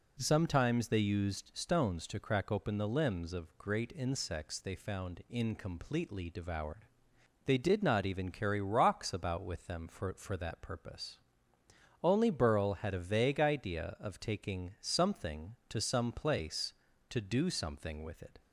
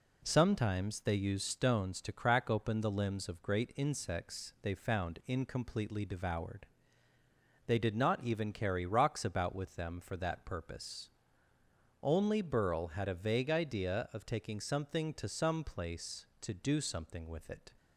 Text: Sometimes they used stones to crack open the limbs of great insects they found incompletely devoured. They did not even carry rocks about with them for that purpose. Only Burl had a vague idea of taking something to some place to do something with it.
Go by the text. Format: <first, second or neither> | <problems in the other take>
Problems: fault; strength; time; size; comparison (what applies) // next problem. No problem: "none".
second | says "for" twice; at 10.1 s